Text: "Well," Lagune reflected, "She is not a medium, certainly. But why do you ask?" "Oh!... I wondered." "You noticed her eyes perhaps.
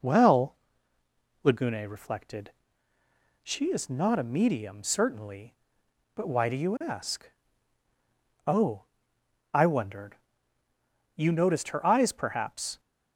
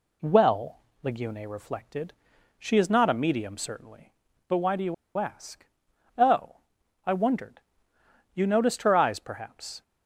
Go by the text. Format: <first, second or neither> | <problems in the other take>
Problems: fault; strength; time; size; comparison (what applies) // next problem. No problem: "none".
first | pauses between "you" and "ask"; slight; at 4.9 s; 0.23 s long